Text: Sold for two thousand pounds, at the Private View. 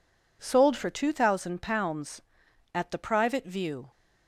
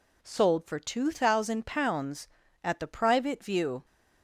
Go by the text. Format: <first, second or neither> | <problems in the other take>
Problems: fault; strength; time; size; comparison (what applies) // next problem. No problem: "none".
neither | none